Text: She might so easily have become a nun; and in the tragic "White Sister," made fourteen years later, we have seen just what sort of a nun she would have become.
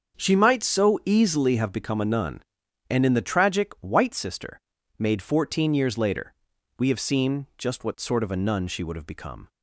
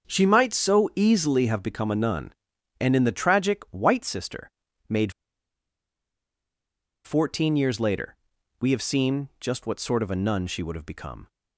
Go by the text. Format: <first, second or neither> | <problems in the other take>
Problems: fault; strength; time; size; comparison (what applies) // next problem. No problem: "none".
first | starts louder than the rest; until 1.1 s; 7 dB; also in the first // pauses between "made" and "fourteen"; strong; at 5.1 s; 1.9 s long